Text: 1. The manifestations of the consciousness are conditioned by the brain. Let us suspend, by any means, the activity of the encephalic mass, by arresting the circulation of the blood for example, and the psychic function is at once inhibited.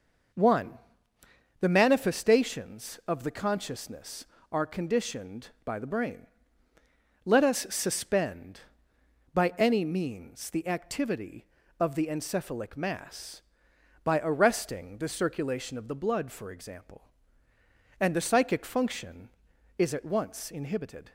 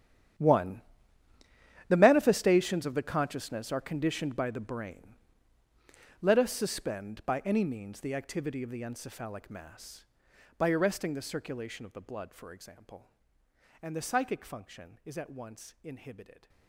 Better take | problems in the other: first | gets quieter; strong; throughout; 17 dB

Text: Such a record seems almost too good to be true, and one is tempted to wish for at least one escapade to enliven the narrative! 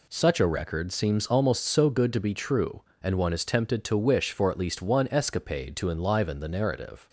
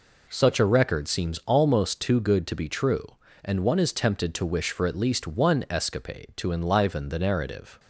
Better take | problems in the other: second | says "so" for "too"; at 1.6 s

